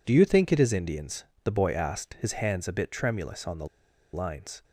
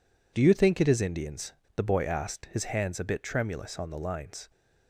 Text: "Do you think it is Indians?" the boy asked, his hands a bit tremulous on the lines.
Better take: second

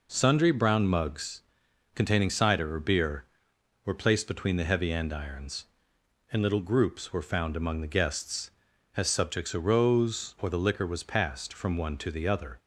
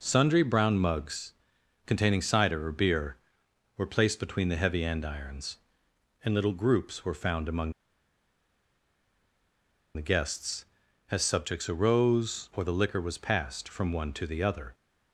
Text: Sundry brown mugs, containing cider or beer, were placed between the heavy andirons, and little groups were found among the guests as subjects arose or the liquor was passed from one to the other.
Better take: first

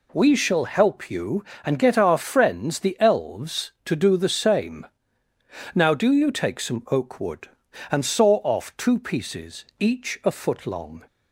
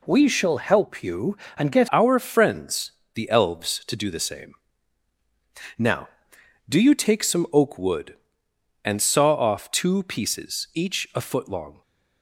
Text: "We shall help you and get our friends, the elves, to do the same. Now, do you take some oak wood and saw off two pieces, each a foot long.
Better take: first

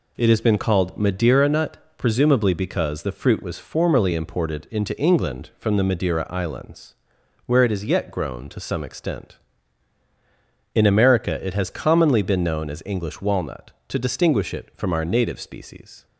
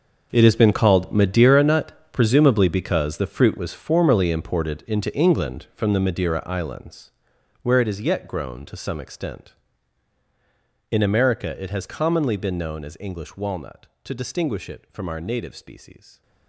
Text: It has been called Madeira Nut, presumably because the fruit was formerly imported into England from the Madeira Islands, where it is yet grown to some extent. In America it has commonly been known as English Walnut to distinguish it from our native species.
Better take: first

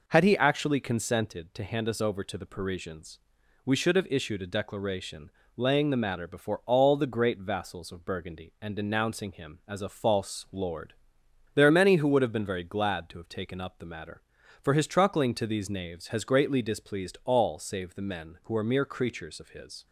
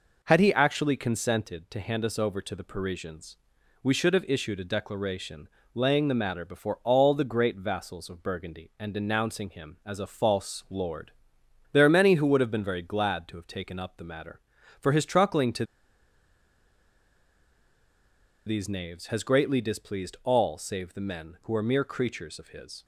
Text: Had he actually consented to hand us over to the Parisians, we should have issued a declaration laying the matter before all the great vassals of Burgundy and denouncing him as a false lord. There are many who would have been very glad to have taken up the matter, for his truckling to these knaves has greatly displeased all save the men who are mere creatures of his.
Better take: first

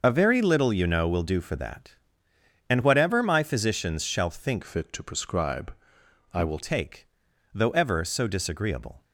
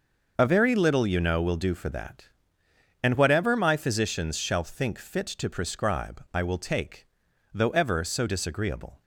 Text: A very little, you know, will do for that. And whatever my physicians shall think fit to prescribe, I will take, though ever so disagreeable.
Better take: second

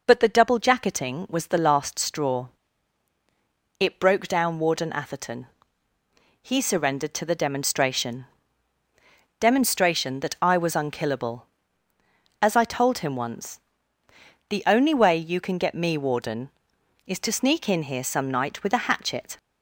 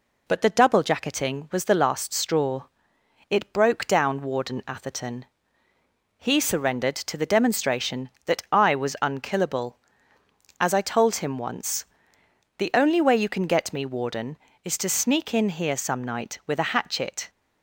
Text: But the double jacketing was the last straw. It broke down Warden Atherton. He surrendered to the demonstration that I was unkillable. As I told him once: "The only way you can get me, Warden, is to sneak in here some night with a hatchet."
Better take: second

